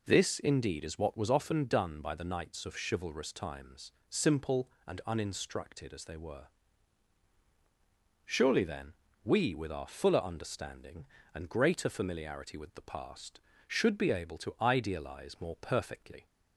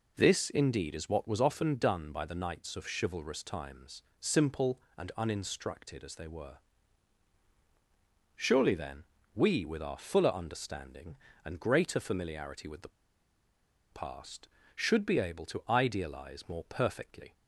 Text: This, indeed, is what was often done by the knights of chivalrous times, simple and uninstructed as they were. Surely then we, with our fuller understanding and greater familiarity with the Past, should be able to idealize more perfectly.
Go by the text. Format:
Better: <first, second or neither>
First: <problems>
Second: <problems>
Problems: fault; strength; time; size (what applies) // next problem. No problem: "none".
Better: first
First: pauses between "then" and "we"; slight; at 8.9 s; 0.30 s long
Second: pauses between "then" and "we"; slight; at 9.0 s; 0.30 s long // pauses between "the" and "Past"; at 12.8 s; 1.0 s long